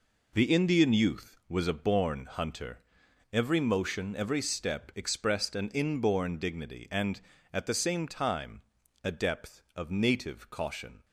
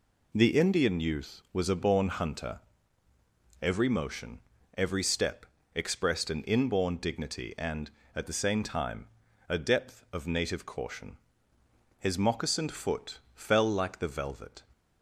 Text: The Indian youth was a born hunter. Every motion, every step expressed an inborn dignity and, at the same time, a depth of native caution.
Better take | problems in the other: first | pauses between "step" and "expressed"; slight; at 5.4 s; 0.30 s long // goes on to say "His moccasined foot fell like the velvet"; strong; from 11.9 s on; 2.6 s long

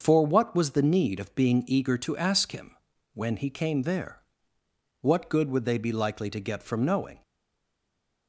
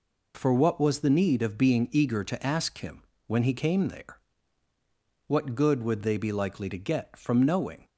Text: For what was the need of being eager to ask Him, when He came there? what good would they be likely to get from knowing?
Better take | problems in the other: second | starts louder than the rest; until 1.0 s; 6 dB // stays silent after the last word; from 7.2 s on; 1.0 s long

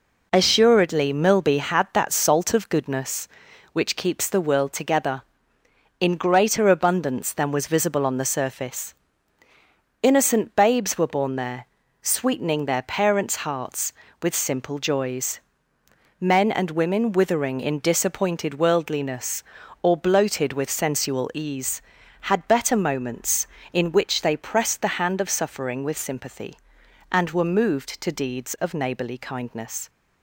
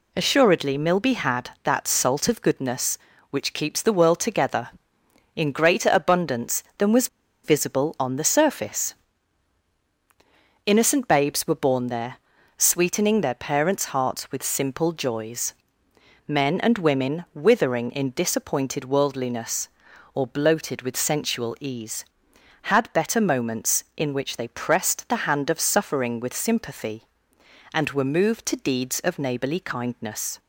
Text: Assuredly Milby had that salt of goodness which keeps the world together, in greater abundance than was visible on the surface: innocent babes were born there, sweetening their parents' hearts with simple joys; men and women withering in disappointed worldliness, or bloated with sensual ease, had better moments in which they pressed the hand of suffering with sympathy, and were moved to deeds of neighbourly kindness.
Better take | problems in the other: first | pauses between "was" and "visible"; at 7.0 s; 0.37 s long

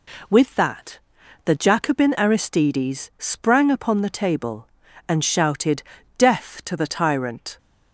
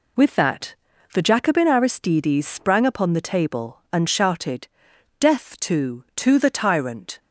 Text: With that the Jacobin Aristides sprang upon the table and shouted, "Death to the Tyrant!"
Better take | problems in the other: first | pauses between "that" and "the"; at 0.7 s; 0.38 s long; noticeable in the first // says "to" twice; at 6.1 s

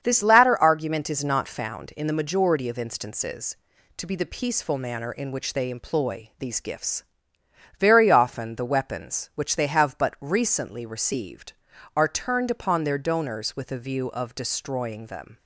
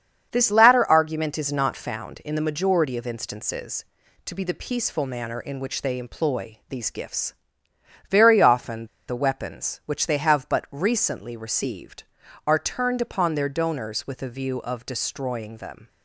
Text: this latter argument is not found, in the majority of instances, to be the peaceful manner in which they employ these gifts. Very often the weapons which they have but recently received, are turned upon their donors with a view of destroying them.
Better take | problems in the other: first | starts louder than the rest; strong; until 1.3 s; 7.5 dB; strong in the first // pauses between "often" and "the"; slight; at 8.8 s; 0.20 s long

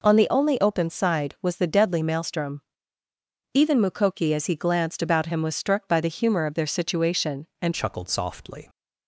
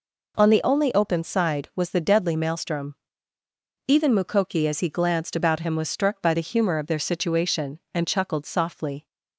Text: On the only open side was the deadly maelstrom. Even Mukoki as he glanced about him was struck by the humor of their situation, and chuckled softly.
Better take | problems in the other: second | changes voice at "chuckled"; from 7.7 s on; 0.9 s long

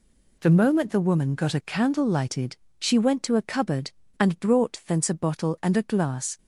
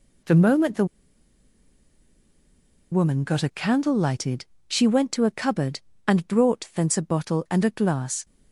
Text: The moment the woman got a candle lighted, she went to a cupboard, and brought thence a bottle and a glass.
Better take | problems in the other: first | pauses between "the" and "woman"; strong; at 0.8 s; 2.0 s long

